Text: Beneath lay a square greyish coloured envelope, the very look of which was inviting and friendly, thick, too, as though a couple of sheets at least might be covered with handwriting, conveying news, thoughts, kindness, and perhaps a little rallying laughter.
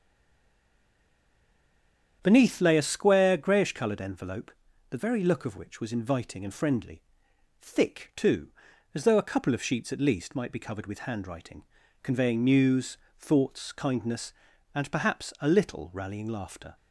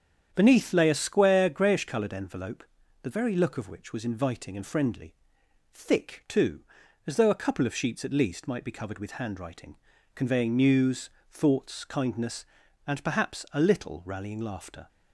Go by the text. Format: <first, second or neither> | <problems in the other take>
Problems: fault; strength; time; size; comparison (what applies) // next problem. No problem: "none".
second | stays silent before the first word; until 2.2 s; 2.2 s long // starts louder than the rest; strong; until 3.2 s; 8.5 dB; strong in the second